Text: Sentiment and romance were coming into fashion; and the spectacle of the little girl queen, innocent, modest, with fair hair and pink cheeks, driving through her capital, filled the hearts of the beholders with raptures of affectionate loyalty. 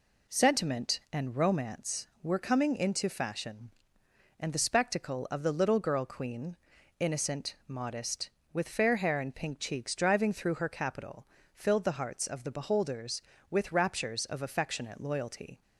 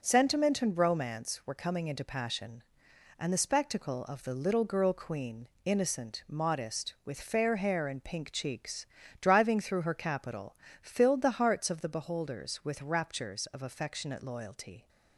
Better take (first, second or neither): first